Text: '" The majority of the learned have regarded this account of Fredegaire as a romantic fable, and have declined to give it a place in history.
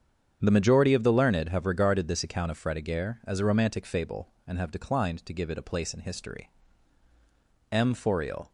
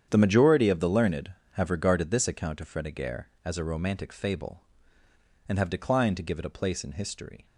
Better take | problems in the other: second | starts louder than the rest; strong; until 1.4 s; 8 dB; strong in the second // goes on to say "M Fauriel"; noticeable; from 7.7 s on; 0.80 s long

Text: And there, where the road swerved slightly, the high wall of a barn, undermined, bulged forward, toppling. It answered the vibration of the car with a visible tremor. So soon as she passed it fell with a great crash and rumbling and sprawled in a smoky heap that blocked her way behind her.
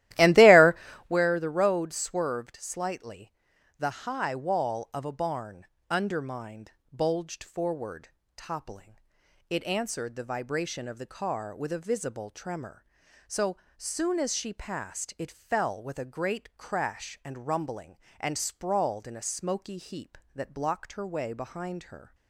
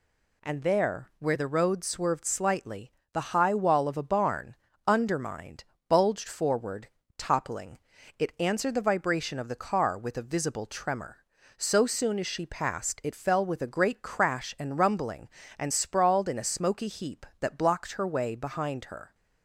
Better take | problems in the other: second | starts louder than the rest; strong; until 1.1 s; 15 dB // pauses between "So" and "soon"; slight; at 13.5 s; 0.20 s long

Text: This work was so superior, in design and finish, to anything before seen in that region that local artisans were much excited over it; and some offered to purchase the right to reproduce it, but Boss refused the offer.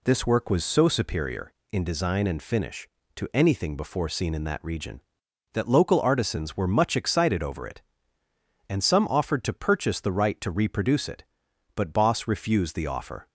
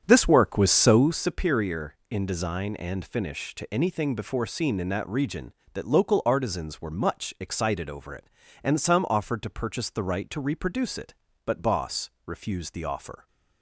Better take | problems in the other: first | starts louder than the rest; strong; until 1.3 s; 8.5 dB // pauses between "Boss" and "refused"; slight; at 12.0 s; 0.16 s long

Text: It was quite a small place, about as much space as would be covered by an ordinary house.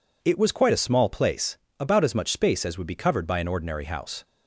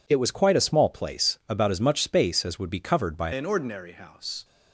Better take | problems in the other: first | changes voice at "an"; from 3.3 s on; 1.1 s long

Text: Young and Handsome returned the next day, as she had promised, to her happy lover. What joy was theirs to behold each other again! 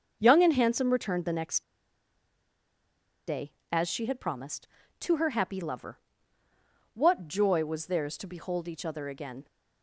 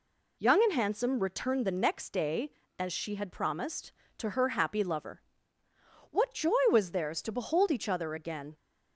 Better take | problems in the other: second | starts louder than the rest; until 1.2 s; 6.5 dB // pauses between "next" and "day"; strong; at 1.6 s; 1.6 s long

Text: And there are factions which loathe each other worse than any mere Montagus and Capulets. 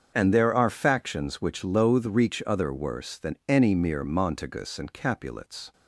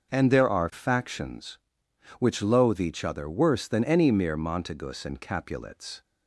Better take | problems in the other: second | starts louder than the rest; until 1.1 s; 7 dB; also in the second // says "reach" for "each"; at 2.0 s

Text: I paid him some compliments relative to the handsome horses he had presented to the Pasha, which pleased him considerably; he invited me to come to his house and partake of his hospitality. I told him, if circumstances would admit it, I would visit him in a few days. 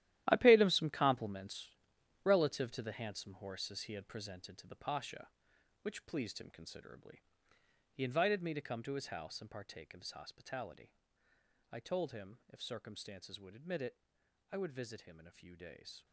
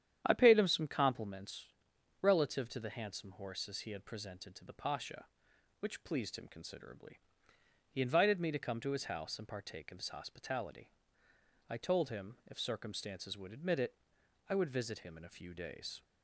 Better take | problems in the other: second | gets quieter; strong; throughout; 12 dB // starts louder than the rest; strong; until 1.2 s; 13 dB; strong in the second // pauses between "compliments" and "relative"; noticeable; at 1.6 s; 0.54 s long; noticeable in the second

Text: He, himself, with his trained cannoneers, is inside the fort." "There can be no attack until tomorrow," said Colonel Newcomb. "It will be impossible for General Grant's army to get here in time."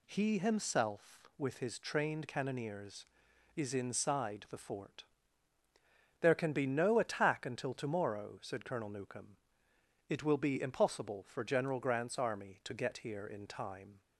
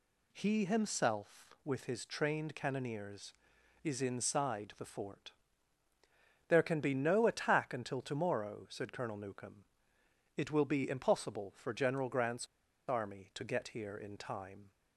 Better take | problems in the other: first | pauses between "Grant's" and "army"; at 12.4 s; 0.41 s long

